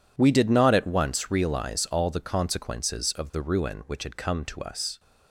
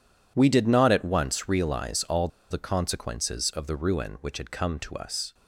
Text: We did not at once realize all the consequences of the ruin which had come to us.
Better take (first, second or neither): first